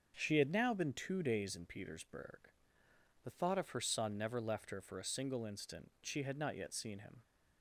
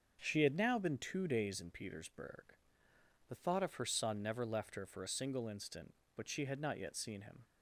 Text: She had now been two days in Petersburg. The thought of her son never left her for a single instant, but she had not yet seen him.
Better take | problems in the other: second | starts louder than the rest; until 1.1 s; 6.5 dB; also in the second // skips "but"; at 5.9 s

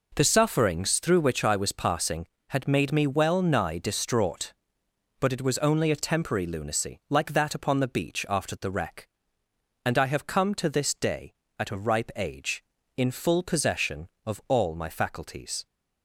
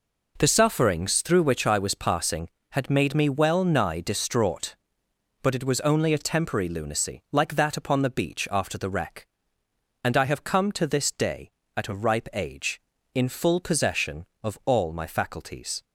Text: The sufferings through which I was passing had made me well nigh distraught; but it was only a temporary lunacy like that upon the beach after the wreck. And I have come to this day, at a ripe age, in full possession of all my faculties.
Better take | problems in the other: neither | none

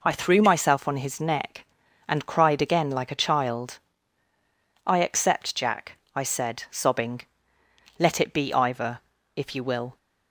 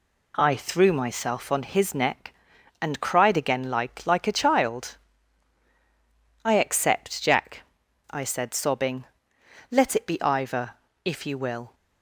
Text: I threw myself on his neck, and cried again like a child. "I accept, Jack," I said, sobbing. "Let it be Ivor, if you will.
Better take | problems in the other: first | says "like" twice; at 4.0 s

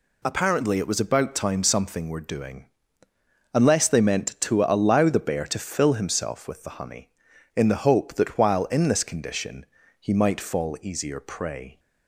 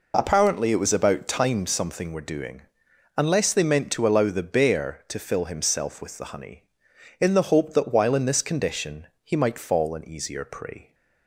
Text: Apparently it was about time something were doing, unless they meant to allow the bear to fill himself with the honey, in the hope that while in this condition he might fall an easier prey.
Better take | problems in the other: second | pauses between "condition" and "he"; slight; at 9.6 s; 0.34 s long; slight in the second // skips "an"; at 10.7 s

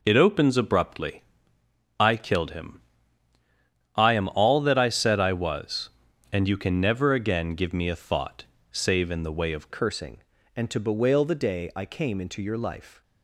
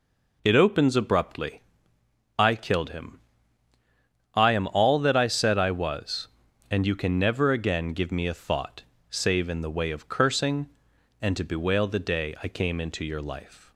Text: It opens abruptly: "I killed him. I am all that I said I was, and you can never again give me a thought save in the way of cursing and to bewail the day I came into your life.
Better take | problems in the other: second | pauses between "thought" and "save"; slight; at 8.4 s; 0.26 s long; slight in the second // changes voice at "cursing"; from 9.7 s on; 3.3 s long

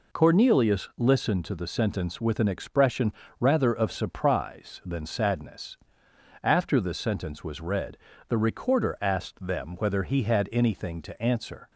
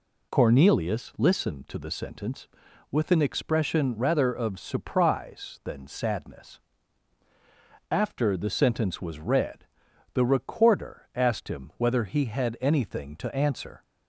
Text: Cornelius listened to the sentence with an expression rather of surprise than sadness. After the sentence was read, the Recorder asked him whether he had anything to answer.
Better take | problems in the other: second | pauses between "expression" and "rather"; slight; at 3.1 s; 0.28 s long // says "them" for "him"; at 9.4 s

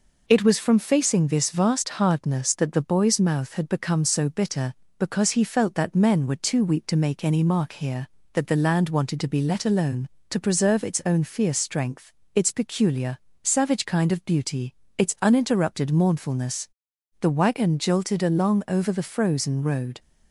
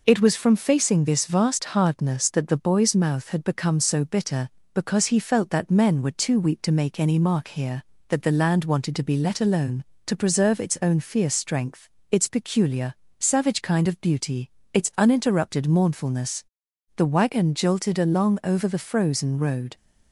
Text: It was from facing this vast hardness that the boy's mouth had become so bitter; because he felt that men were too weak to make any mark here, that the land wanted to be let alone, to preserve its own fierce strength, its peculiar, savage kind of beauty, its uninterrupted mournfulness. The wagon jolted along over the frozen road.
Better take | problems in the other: neither | none

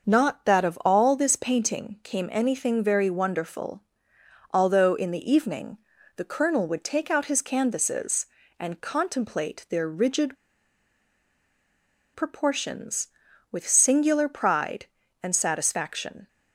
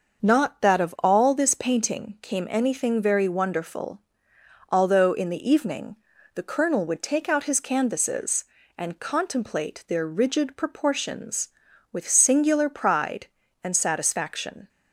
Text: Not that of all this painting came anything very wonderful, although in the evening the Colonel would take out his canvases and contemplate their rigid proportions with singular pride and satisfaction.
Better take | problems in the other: second | starts louder than the rest; until 1.1 s; 6 dB; also in the second // pauses between "evening" and "the"; at 5.7 s; 0.38 s long; also in the second // pauses between "rigid" and "proportions"; strong; at 10.3 s; 1.7 s long

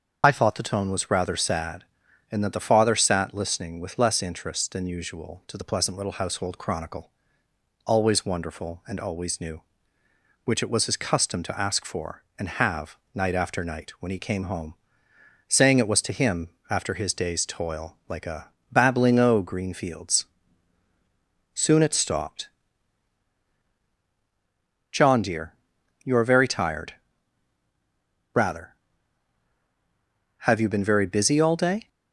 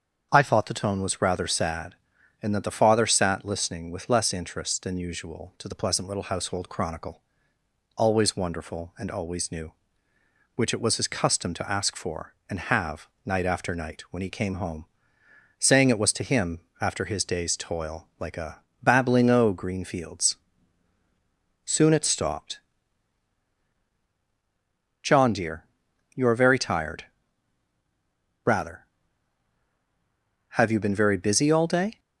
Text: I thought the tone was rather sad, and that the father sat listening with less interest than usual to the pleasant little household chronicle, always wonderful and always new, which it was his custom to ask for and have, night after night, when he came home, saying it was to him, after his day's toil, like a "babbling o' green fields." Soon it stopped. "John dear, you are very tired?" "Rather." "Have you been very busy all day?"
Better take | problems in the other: second | loses the start of "I"; at 0.2 s; 40 ms // starts louder than the rest; until 1.2 s; 7 dB; strong in the second // pauses between "a" and "babbling"; slight; at 18.4 s; 0.22 s long; slight in the second

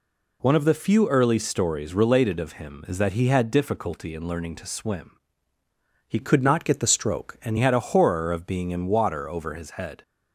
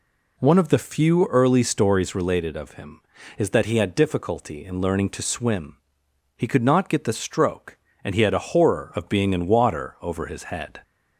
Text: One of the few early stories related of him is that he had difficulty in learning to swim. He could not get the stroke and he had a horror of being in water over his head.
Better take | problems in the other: second | changes voice from "could" to "and"; from 6.1 to 7.5 s; 1.4 s long

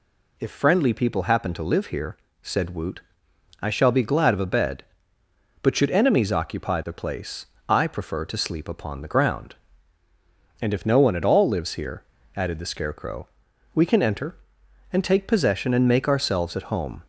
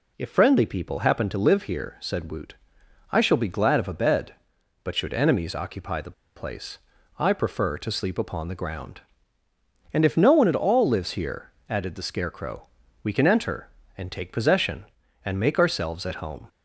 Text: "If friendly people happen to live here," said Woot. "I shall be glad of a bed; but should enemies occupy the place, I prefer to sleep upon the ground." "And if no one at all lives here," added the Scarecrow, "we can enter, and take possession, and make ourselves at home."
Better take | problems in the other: first | pauses between "the" and "place"; slight; at 6.1 s; 0.22 s long

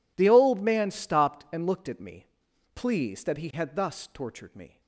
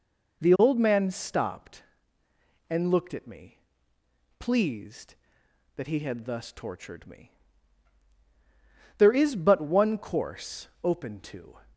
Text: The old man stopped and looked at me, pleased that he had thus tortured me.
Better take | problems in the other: first | goes on to say "There is but one course open to"; strong; from 8.9 s on; 2.6 s long

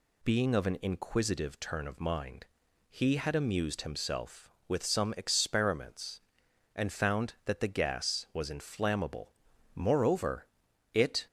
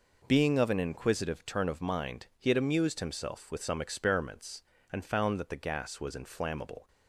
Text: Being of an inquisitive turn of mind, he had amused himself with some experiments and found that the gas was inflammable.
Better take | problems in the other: second | goes on to say "Moreover it"; from 9.7 s on; 1.5 s long

